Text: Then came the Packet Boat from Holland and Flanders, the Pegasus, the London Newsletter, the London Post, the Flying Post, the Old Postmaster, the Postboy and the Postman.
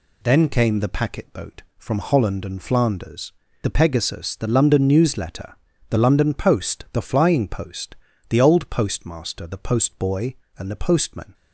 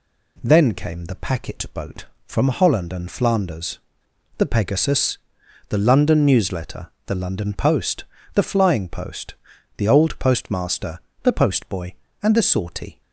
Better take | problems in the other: first | says "Sortie" for "Postman"; at 12.4 s

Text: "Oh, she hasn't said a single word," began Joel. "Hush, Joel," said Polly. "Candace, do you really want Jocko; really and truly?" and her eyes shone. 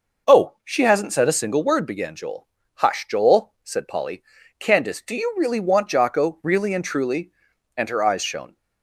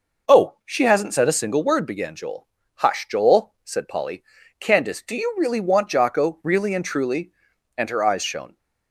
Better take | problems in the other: neither | none

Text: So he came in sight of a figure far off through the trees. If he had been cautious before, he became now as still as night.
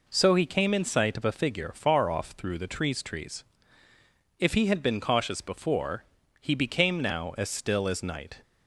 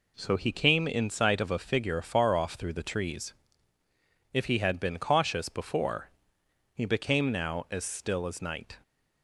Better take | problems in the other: second | says "trees" twice; at 3.0 s

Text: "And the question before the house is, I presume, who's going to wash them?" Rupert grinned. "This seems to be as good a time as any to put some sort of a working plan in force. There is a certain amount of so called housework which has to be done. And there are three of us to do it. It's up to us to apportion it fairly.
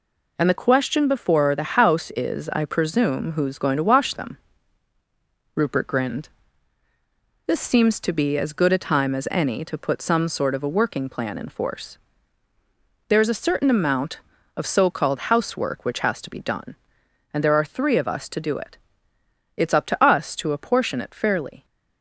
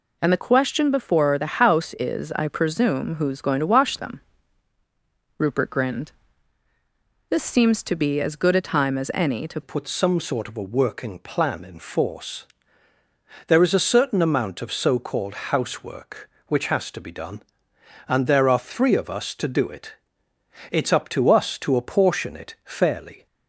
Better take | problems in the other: first | changes voice at "put"; from 9.6 s on; 13.6 s long

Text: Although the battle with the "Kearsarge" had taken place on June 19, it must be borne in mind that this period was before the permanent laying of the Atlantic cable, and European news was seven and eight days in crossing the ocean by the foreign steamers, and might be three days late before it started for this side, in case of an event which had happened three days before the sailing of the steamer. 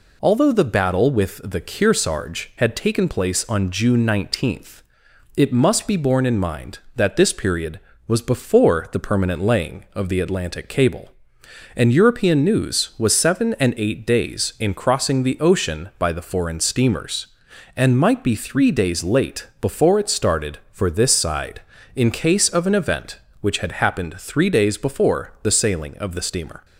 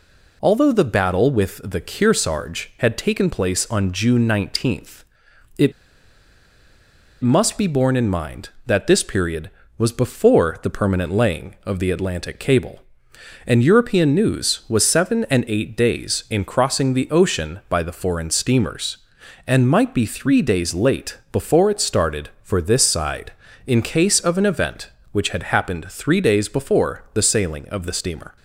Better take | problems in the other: first | pauses between "it" and "must"; strong; at 5.7 s; 1.4 s long

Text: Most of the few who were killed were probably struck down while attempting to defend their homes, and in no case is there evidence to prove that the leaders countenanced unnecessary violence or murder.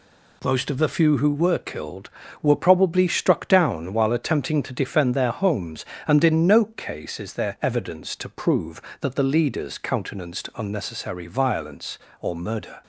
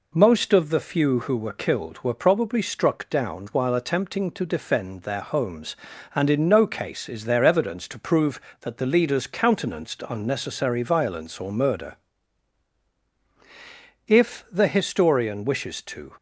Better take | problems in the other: first | goes on to say "If the historian wishes to"; strong; from 14.0 s on; 2.0 s long

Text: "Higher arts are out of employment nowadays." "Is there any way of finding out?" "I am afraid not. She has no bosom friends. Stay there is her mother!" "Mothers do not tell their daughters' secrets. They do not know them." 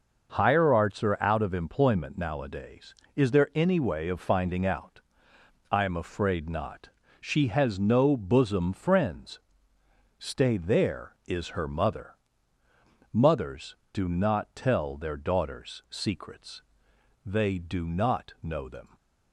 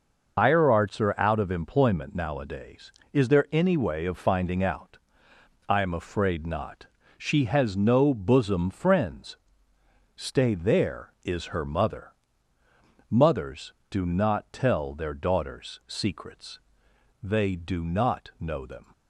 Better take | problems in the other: first | loses the start of "Higher"; at 0.3 s; 105 ms

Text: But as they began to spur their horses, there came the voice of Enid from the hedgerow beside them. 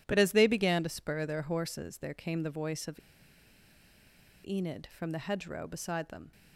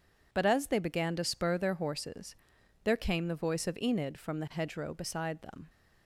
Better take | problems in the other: second | pauses between "of" and "Enid"; strong; at 2.9 s; 1.4 s long

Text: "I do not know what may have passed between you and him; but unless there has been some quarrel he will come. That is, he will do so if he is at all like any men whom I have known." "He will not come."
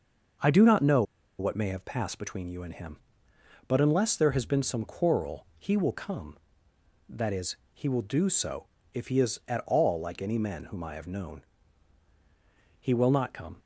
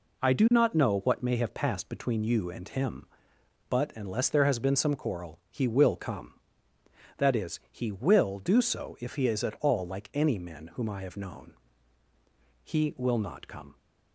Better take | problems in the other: second | starts louder than the rest; noticeable; until 1.7 s; 6 dB // pauses between "know" and "what"; at 1.0 s; 0.36 s long // pauses between "so" and "if"; slight; at 8.6 s; 0.26 s long

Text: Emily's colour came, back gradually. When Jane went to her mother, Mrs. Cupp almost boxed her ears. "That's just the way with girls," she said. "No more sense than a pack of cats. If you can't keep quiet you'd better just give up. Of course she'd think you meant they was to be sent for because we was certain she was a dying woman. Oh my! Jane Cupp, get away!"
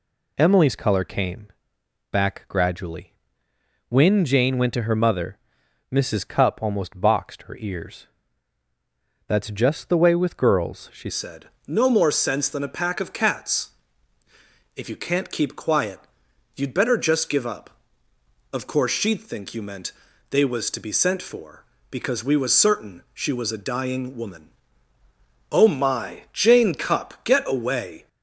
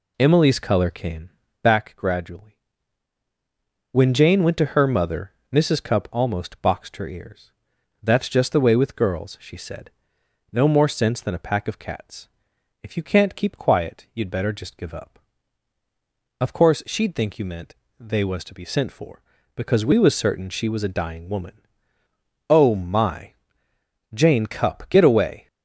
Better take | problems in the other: second | changes voice at "said"; from 11.0 s on; 17.0 s long // pauses between "quiet" and "you'd"; noticeable; at 15.9 s; 0.56 s long // pauses between "meant" and "they"; at 19.9 s; 0.40 s long; slight in the second

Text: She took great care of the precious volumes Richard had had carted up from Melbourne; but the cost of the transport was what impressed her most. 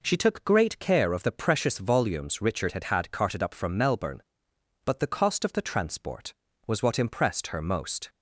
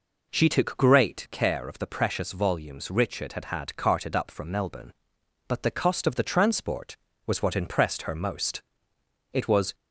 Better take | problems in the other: first | goes on to say "It was"; slight; from 9.3 s on; 0.42 s long

